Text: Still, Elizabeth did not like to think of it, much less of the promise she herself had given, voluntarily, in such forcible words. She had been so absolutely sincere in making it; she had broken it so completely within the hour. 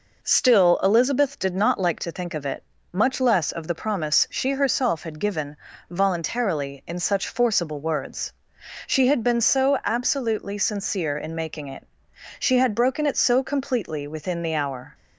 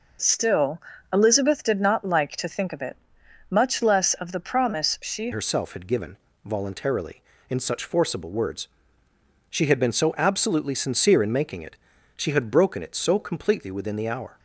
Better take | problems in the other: first | changes voice at "herself"; from 5.3 s on; 9.0 s long

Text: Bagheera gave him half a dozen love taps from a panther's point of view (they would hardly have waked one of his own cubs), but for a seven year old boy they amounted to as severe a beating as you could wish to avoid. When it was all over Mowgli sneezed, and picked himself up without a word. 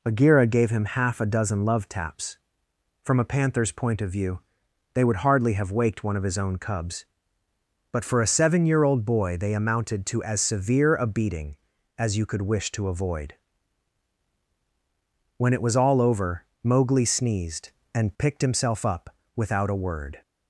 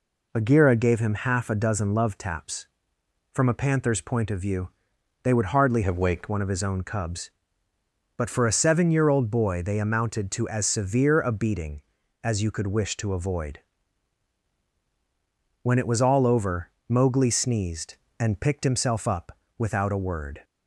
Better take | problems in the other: first | changes voice from "have" to "waked"; from 5.8 to 6.2 s; 0.4 s long // pauses between "over" and "Mowgli"; slight; at 16.6 s; 0.18 s long; slight in the first // pauses between "up" and "without"; slight; at 19.3 s; 0.22 s long; slight in the first

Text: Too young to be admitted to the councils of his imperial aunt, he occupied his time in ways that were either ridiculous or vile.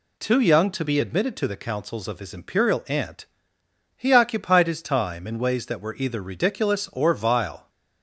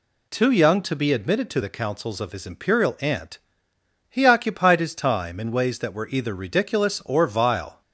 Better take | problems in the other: neither | none

